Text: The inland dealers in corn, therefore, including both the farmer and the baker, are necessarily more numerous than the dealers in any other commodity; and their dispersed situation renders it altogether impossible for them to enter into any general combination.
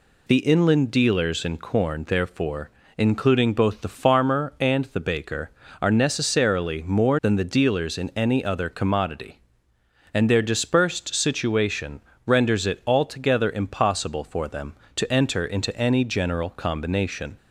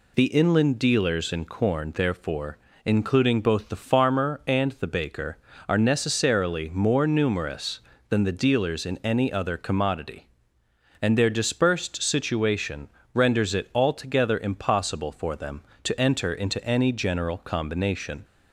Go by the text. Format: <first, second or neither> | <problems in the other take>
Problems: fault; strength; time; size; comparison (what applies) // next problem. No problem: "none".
second | skips "numerous"; at 7.1 s // pauses between "situation" and "renders"; slight; at 11.9 s; 0.26 s long; slight in the second